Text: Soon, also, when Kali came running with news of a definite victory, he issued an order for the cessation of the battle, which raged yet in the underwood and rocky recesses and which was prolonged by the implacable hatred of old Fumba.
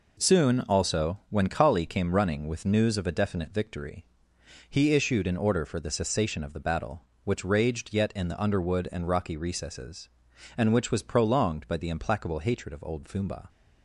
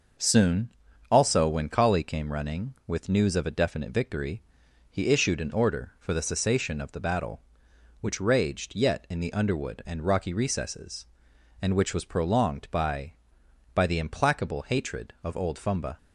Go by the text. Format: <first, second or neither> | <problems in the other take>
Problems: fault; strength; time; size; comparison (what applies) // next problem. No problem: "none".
first | starts louder than the rest; until 1.6 s; 6 dB // says "by" twice; at 13.7 s